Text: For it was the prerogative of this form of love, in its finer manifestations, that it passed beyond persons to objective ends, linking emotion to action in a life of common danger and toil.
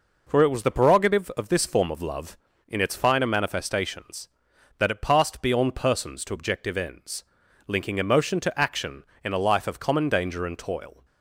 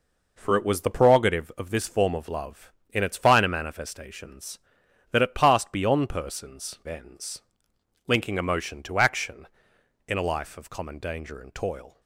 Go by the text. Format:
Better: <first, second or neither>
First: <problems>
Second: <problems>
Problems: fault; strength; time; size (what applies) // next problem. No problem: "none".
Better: first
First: none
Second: skips "to objective"; at 6.8 s